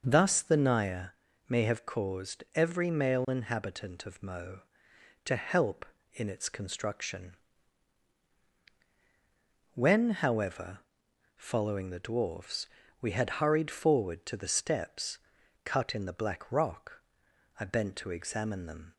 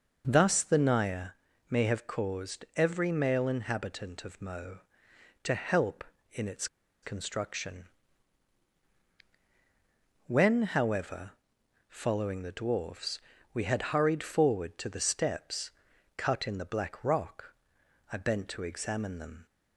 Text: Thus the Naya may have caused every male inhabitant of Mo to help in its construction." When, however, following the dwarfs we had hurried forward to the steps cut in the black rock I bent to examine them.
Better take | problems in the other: first | pauses between "Naya" and "may"; at 1.2 s; 0.42 s long; also in the first // pauses between "its" and "construction"; at 6.6 s; 0.36 s long // pauses between "dwarfs" and "we"; slight; at 13.1 s; 0.34 s long; slight in the first // pauses between "steps" and "cut"; noticeable; at 15.6 s; 0.48 s long; noticeable in the first // pauses between "rock" and "I"; noticeable; at 17.5 s; 0.58 s long; noticeable in the first

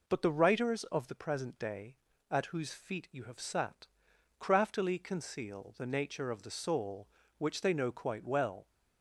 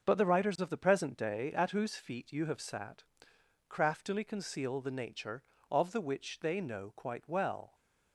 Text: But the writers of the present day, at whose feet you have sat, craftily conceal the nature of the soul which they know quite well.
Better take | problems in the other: first | starts louder than the rest; until 1.0 s; 6 dB // skips "soul"; at 6.0 s

